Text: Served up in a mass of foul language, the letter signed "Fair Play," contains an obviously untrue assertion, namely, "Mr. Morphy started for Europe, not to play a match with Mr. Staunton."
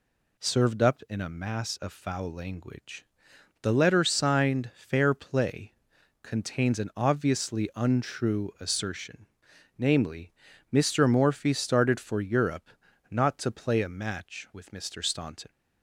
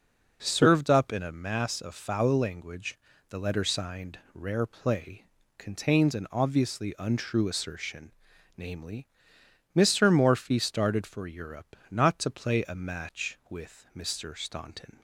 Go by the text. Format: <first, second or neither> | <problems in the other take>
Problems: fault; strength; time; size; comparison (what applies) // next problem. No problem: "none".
first | says "Rare" for "Fair"; at 4.3 s